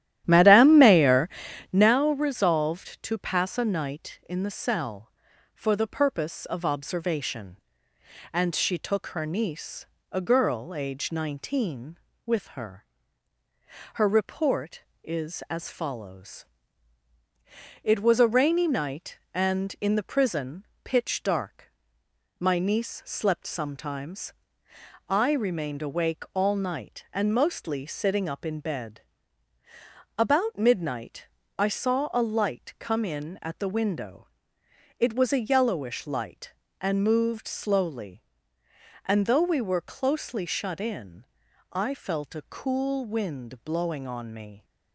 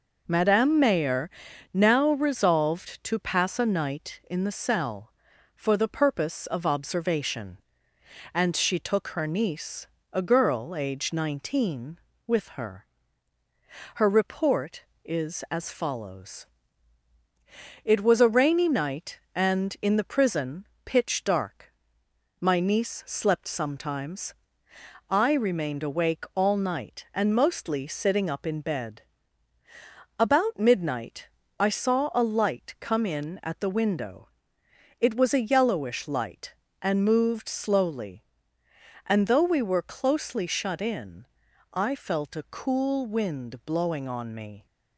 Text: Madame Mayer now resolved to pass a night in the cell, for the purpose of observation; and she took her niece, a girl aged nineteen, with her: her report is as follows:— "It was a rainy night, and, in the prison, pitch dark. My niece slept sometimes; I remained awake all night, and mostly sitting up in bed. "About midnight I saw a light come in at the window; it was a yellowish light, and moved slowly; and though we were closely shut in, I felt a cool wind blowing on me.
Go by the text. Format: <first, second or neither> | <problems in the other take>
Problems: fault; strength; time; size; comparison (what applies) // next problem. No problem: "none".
second | starts louder than the rest; strong; until 1.9 s; 13 dB // pauses between "Mayer" and "now"; at 1.2 s; 0.42 s long; also in the second // pauses between "midnight" and "I"; slight; at 31.2 s; 0.32 s long; slight in the second